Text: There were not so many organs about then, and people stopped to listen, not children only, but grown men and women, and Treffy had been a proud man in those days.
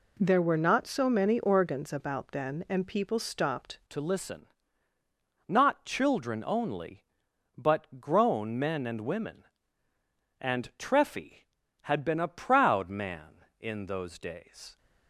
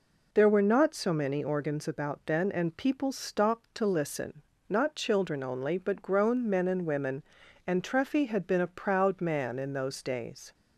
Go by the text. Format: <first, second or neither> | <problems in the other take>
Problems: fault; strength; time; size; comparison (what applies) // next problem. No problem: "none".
second | changes voice at "to"; from 3.8 s on; 10.9 s long